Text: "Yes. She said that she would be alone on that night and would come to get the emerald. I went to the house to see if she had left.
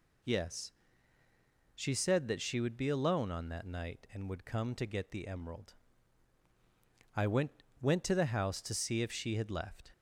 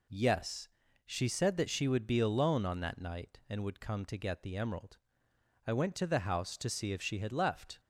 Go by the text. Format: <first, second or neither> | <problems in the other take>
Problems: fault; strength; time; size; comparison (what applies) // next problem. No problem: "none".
second | says "went" twice; at 7.8 s